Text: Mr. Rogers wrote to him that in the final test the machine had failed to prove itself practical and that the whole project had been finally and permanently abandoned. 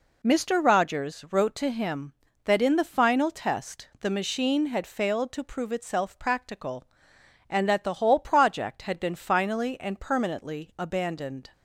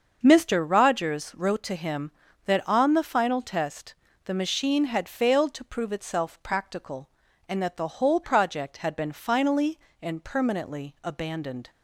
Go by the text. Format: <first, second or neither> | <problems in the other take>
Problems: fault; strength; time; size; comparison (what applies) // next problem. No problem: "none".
first | starts louder than the rest; until 1.2 s; 6.5 dB // says "on" for "in"; at 2.6 s // pauses between "test" and "the"; slight; at 3.9 s; 0.30 s long